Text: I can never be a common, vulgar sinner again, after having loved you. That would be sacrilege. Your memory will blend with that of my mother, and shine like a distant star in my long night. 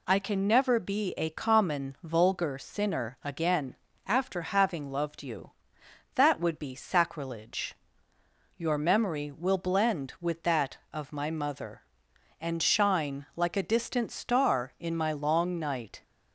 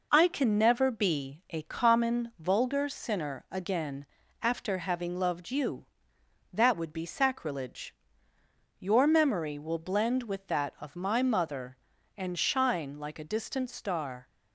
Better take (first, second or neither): first